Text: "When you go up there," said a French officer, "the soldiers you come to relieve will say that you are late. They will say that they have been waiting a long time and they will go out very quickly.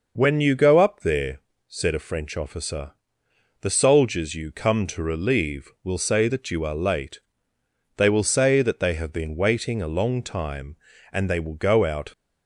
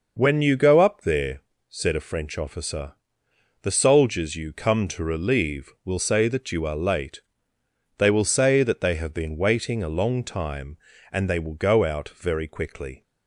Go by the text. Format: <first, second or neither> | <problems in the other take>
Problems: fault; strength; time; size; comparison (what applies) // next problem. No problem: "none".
second | stops before "very quickly"; at 12.1 s